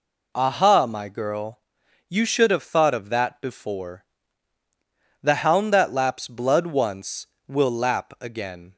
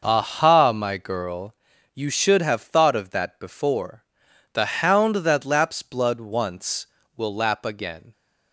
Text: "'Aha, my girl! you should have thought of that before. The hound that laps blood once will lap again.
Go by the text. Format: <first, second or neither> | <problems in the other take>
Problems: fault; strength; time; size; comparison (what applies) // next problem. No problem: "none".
neither | none